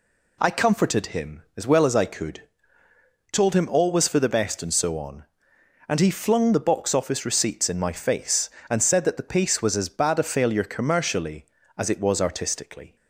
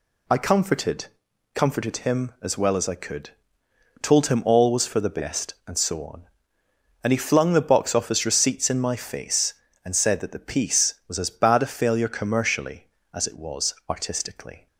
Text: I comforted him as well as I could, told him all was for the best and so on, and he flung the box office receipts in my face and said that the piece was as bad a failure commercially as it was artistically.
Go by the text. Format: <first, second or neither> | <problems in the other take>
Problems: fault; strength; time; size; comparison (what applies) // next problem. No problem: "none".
first | says "comforted" twice; at 1.5 s // pauses between "was" and "artistically"; slight; at 13.7 s; 0.16 s long